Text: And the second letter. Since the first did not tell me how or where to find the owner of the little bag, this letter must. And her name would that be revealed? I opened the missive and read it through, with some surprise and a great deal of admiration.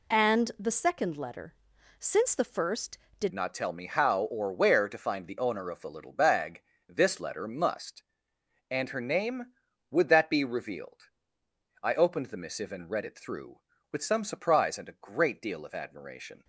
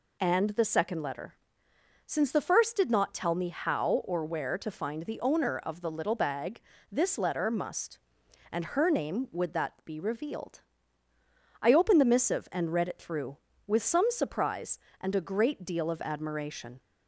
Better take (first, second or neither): second